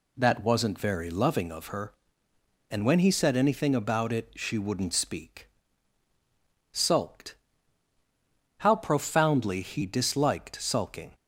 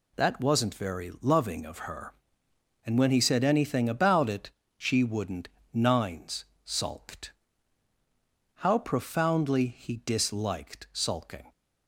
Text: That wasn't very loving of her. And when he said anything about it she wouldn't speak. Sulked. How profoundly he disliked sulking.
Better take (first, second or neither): first